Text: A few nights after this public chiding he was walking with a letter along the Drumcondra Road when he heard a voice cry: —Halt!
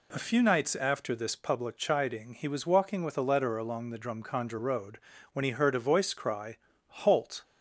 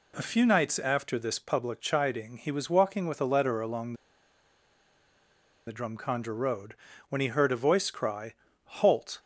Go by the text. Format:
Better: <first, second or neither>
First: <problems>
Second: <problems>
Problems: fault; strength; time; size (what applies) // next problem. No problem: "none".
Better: first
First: pauses between "Road" and "when"; slight; at 4.9 s; 0.36 s long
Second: pauses between "along" and "the"; strong; at 3.9 s; 1.7 s long // pauses between "Road" and "when"; slight; at 6.7 s; 0.36 s long